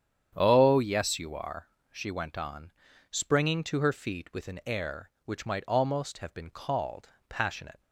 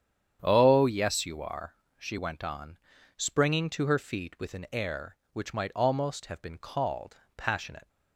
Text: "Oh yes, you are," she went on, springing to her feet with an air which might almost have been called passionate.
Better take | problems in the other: neither | starts louder than the rest; strong; the same in both // pauses between "called" and "passionate"; slight; the same in both

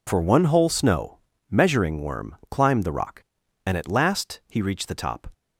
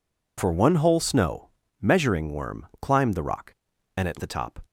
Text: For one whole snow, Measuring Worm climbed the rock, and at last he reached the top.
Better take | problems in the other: first | skips "last he reached"; at 4.1 s

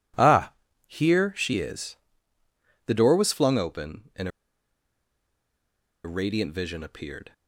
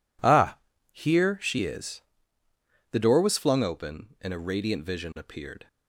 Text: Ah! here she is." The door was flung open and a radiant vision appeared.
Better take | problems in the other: second | pauses between "and" and "a"; strong; at 4.2 s; 1.7 s long

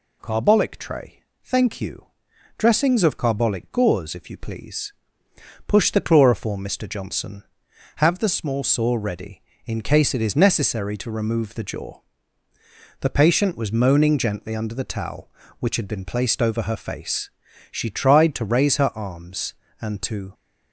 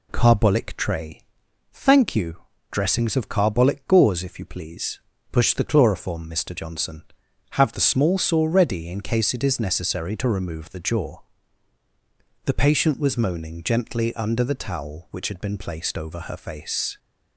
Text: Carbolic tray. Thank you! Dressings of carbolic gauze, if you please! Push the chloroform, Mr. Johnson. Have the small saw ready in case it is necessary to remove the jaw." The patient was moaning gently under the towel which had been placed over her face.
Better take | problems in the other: second | goes on to say "She tried to raise her arms and to"; strong; from 17.7 s on; 2.6 s long

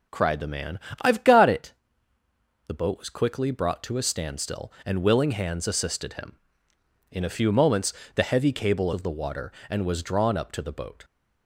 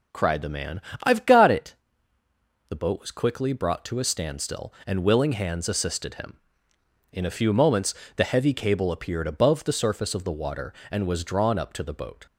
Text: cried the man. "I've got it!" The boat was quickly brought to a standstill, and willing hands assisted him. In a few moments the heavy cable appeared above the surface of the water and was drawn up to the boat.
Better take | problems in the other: second | pauses between "moments" and "the"; slight; at 7.9 s; 0.22 s long; slight in the second // skips "appeared above the surface"; at 8.9 s

